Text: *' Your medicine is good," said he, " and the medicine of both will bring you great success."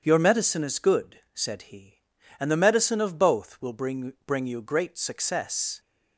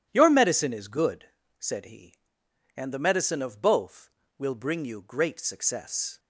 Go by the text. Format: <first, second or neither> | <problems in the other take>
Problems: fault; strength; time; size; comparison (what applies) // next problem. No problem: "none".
second | starts louder than the rest; strong; until 1.0 s; 8 dB; strong in the second // says "bring" twice; at 4.2 s